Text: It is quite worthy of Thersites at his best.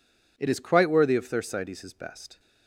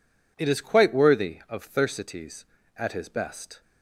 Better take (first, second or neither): second